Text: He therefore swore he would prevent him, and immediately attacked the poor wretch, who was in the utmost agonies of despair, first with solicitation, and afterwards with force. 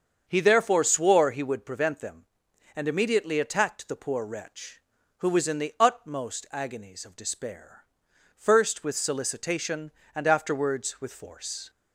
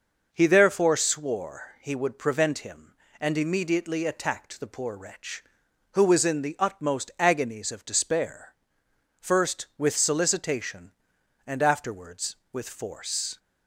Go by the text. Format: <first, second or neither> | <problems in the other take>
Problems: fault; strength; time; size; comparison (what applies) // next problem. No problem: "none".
second | starts louder than the rest; until 1.2 s; 7 dB // says "them" for "him"; at 1.9 s